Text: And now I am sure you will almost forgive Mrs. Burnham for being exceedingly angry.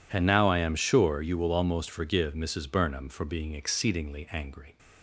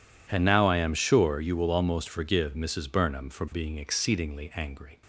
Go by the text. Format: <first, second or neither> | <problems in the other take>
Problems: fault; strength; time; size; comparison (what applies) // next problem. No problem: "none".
neither | none